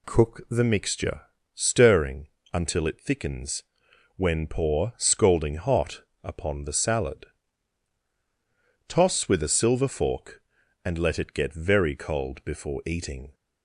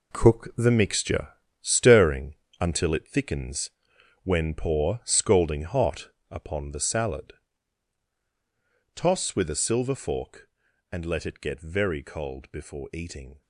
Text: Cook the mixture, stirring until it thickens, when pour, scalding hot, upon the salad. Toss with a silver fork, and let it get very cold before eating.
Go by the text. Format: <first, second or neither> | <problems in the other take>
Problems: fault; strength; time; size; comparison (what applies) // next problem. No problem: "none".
first | gets quieter; strong; throughout; 11 dB // pauses between "stirring" and "until"; slight; at 2.3 s; 0.24 s long; slight in the first